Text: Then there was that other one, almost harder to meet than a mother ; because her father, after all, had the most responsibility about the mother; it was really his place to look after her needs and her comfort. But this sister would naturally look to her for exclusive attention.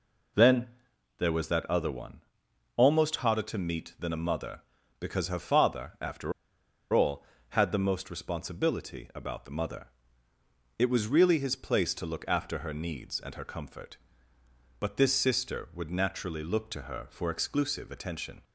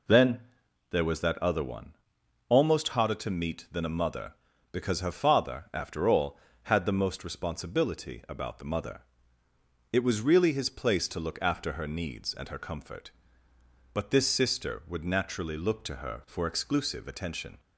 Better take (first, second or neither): second